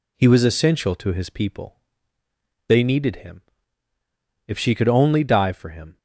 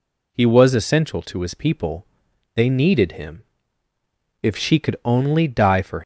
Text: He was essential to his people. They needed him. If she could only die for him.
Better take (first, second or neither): first